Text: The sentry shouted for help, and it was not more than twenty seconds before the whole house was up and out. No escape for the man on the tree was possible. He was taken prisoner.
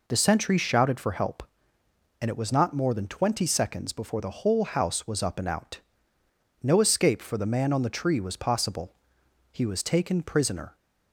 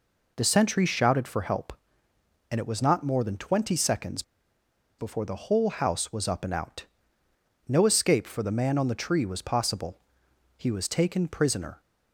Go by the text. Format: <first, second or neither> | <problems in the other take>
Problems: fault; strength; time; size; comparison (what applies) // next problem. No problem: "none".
first | pauses between "seconds" and "before"; noticeable; at 4.2 s; 0.76 s long